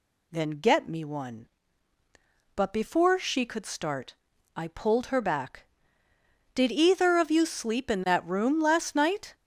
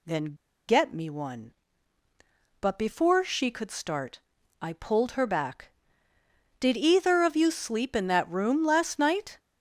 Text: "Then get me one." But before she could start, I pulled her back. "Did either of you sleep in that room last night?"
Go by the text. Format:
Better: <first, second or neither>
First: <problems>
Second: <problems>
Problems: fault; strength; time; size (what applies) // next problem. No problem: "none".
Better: first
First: none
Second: pauses between "Then" and "get"; slight; at 0.3 s; 0.36 s long